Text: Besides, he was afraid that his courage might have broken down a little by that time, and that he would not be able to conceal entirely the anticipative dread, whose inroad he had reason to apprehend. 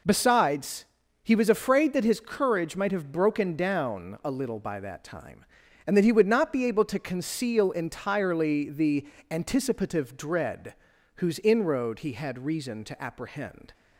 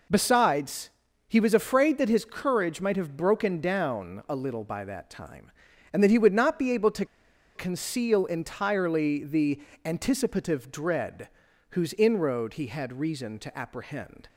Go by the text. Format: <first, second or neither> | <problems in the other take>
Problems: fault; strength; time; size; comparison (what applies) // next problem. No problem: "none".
first | pauses between "to" and "conceal"; noticeable; at 7.0 s; 0.51 s long // pauses between "the" and "anticipative"; slight; at 9.6 s; 0.24 s long; slight in the first